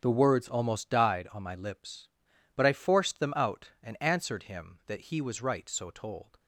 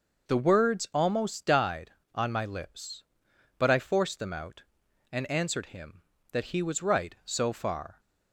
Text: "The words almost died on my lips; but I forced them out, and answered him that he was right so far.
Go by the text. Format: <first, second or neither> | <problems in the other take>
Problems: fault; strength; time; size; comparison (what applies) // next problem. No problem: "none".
second | starts louder than the rest; strong; until 1.0 s; 8 dB // says "told" for "far"; at 5.9 s